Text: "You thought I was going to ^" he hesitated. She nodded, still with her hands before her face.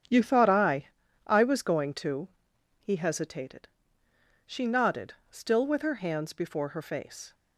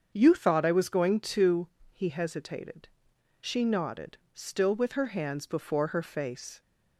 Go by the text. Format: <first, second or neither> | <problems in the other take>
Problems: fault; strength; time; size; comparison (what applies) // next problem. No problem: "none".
second | starts louder than the rest; strong; until 1.4 s; 8 dB; also in the second // says "I" twice; at 1.2 s